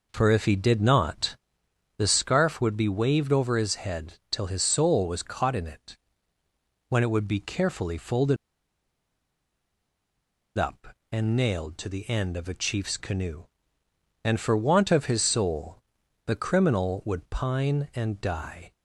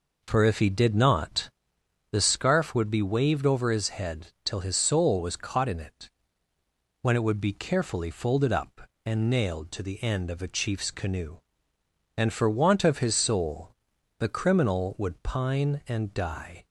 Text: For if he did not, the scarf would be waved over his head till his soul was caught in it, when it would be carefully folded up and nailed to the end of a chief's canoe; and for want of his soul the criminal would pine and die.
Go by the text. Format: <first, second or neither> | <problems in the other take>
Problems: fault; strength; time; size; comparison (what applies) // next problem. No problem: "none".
second | pauses between "folded" and "up"; strong; at 8.3 s; 2.2 s long // pauses between "soul" and "the"; at 15.8 s; 0.44 s long; also in the second